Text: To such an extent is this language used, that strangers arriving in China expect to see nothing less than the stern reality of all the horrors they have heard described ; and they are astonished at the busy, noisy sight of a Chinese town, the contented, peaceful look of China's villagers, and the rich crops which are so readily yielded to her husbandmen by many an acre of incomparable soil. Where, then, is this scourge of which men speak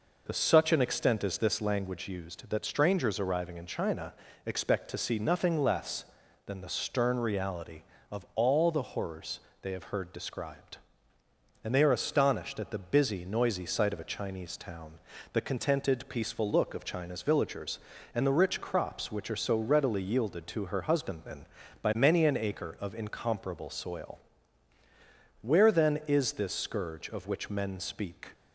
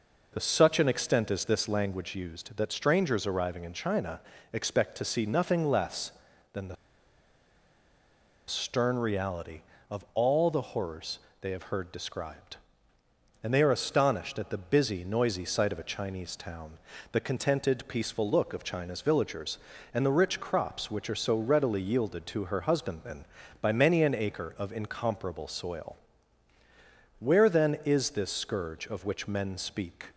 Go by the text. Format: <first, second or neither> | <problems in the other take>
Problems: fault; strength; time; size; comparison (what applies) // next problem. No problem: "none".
first | pauses between "China" and "expect"; slight; at 4.1 s; 0.32 s long; slight in the first // pauses between "the" and "stern"; strong; at 6.7 s; 1.7 s long // pauses between "horrors" and "they"; slight; at 11.1 s; 0.22 s long; slight in the first